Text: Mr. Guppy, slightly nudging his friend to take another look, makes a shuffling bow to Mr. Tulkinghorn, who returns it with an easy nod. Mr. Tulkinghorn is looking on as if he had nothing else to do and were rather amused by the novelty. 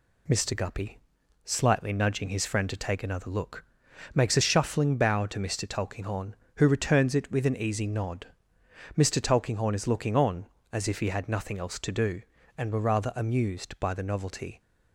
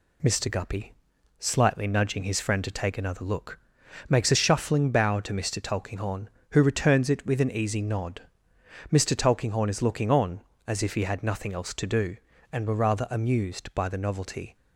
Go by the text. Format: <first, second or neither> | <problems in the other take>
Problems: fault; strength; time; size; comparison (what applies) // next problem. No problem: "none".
neither | none